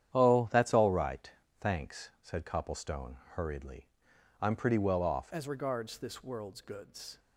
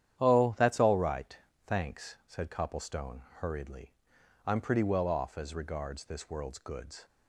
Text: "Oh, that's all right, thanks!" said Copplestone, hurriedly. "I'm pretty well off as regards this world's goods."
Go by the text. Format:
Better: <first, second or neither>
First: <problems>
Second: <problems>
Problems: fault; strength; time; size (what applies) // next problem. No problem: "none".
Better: second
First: starts louder than the rest; strong; until 1.1 s; 9.5 dB // changes voice at "as"; from 5.3 s on; 1.8 s long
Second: starts louder than the rest; strong; until 1.2 s; 10 dB